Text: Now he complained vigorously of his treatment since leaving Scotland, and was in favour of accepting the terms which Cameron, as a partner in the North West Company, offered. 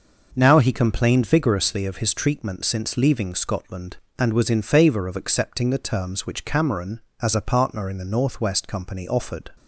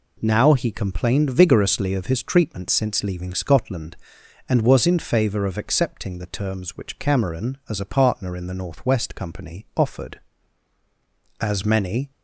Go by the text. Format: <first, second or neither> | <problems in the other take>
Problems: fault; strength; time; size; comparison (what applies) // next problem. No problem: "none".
first | goes on to say "As many"; noticeable; from 11.4 s on; 0.70 s long